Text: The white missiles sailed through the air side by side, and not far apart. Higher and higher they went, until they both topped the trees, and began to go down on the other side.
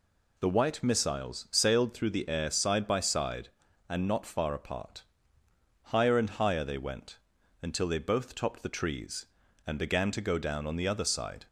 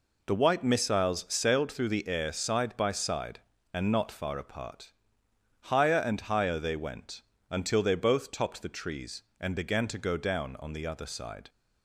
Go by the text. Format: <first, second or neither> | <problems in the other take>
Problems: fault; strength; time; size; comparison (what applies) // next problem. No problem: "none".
neither | none